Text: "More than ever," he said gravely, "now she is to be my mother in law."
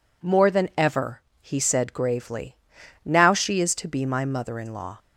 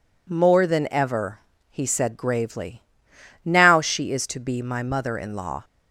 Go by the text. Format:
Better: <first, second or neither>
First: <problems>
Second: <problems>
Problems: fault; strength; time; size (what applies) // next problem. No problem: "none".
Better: neither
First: none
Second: none